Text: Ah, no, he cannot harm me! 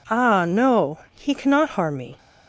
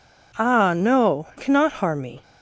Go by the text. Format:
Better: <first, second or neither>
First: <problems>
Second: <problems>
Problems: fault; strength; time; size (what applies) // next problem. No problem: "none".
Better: first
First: none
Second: skips "he"; at 1.3 s